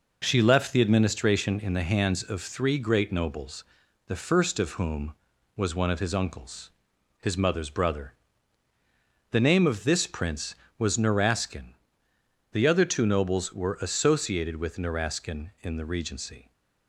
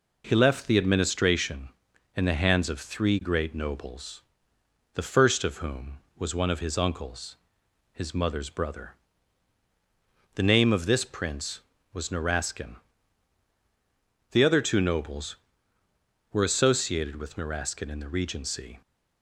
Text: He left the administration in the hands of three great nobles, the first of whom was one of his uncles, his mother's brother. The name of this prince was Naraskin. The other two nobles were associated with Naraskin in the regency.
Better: second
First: says "She" for "He"; at 0.2 s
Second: none

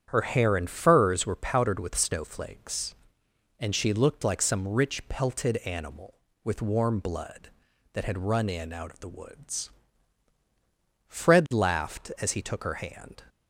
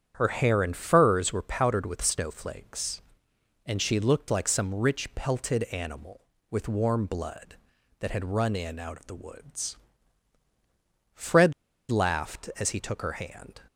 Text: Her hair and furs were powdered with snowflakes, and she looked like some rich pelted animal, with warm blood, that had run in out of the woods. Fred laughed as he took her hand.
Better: first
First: starts louder than the rest; strong; until 1.0 s; 8.5 dB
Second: starts louder than the rest; strong; until 1.1 s; 8.5 dB // pauses between "Fred" and "laughed"; at 11.5 s; 0.36 s long

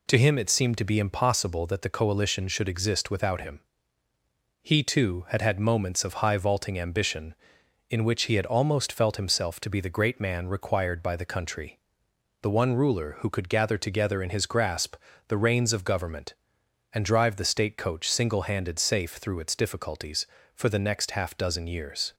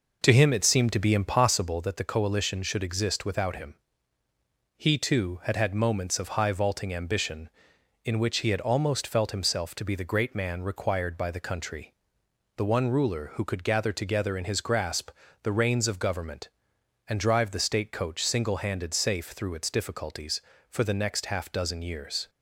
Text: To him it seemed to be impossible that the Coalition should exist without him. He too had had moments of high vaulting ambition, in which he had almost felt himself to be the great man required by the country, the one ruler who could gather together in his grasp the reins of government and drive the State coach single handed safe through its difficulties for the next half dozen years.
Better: first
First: pauses between "grasp" and "the"; slight; at 14.9 s; 0.34 s long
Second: starts louder than the rest; noticeable; until 1.7 s; 5 dB // pauses between "grasp" and "the"; slight; at 15.0 s; 0.34 s long

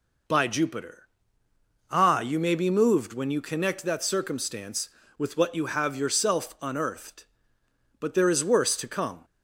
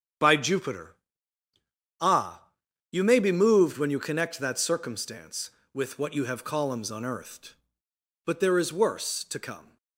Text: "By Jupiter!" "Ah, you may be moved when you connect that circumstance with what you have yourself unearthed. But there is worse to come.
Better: first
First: none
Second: starts louder than the rest; strong; until 2.2 s; 8.5 dB // says "columns" for "yourself"; at 6.4 s

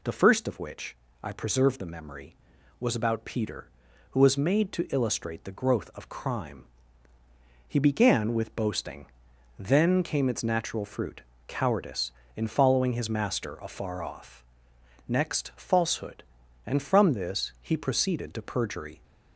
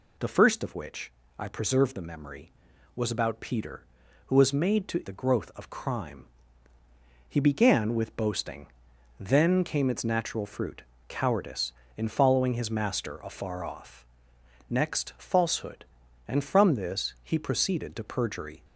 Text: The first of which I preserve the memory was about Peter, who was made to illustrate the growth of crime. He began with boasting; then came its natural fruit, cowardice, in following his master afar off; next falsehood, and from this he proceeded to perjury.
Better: first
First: pauses between "which" and "I"; slight; at 0.9 s; 0.26 s long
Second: pauses between "which" and "I"; slight; at 1.1 s; 0.26 s long // skips "illustrate"; at 5.0 s

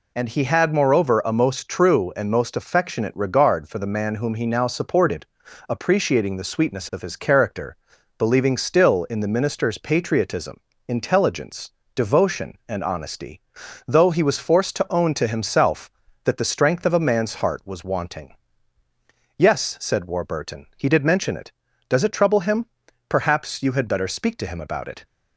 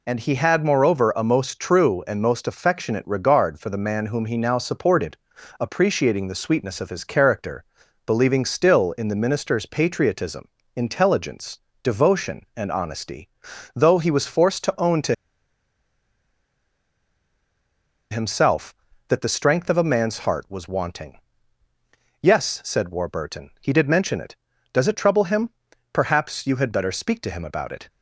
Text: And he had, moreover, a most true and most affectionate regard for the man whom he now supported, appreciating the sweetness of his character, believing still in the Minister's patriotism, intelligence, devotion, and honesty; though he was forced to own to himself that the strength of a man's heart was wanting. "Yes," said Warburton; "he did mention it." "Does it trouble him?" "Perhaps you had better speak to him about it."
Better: first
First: none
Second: pauses between "to" and "himself"; strong; at 15.1 s; 2.9 s long

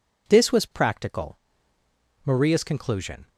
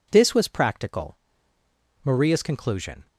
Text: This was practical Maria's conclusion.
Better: neither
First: pauses between "practical" and "Maria's"; noticeable; at 1.3 s; 0.84 s long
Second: pauses between "practical" and "Maria's"; noticeable; at 1.1 s; 0.84 s long

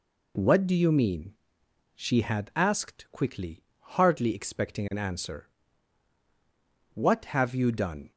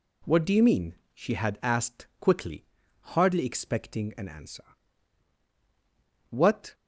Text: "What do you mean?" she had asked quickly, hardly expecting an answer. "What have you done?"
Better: first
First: none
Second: stops before "have you done"; at 6.7 s

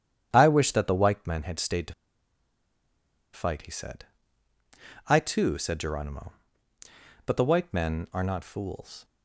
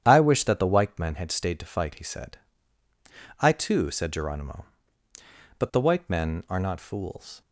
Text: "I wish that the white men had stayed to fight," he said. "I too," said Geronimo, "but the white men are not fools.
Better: second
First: starts louder than the rest; strong; until 1.3 s; 9.5 dB // pauses between "to" and "fight"; strong; at 1.9 s; 1.4 s long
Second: starts louder than the rest; strong; until 1.0 s; 9.5 dB

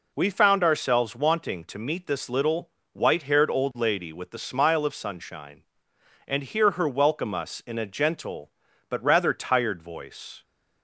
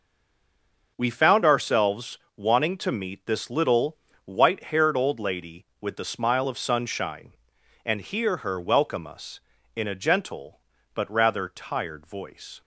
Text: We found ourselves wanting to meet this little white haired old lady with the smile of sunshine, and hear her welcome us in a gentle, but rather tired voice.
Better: first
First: pauses between "little" and "white"; slight; at 2.6 s; 0.24 s long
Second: stays silent before the first word; until 0.9 s; 0.9 s long // pauses between "ourselves" and "wanting"; slight; at 2.1 s; 0.18 s long // pauses between "little" and "white"; slight; at 3.9 s; 0.30 s long

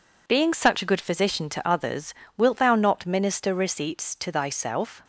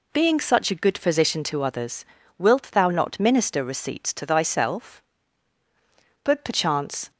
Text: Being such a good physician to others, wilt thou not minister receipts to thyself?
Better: first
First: none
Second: goes on to say "But perchance"; noticeable; from 6.2 s on; 0.86 s long

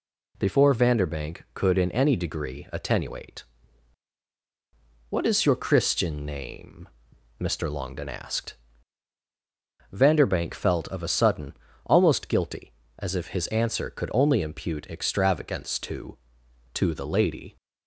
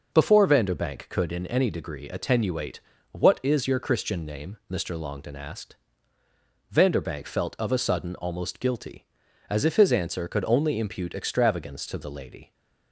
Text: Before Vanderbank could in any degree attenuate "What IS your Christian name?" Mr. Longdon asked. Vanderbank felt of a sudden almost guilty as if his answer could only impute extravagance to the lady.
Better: second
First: pauses between "attenuate" and "What"; strong; at 3.4 s; 1.6 s long // pauses between "sudden" and "almost"; slight; at 11.5 s; 0.32 s long // says "to" twice; at 16.7 s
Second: pauses between "attenuate" and "What"; slight; at 2.8 s; 0.32 s long

